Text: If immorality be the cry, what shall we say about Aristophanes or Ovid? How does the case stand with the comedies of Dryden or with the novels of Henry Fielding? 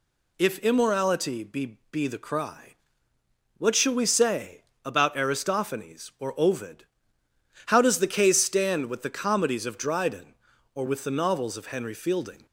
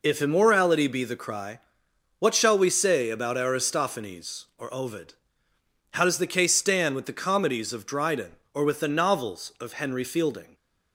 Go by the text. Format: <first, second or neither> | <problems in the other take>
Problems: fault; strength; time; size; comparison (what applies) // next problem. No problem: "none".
second | says "be" twice; at 1.9 s // pauses between "say" and "about"; slight; at 4.6 s; 0.20 s long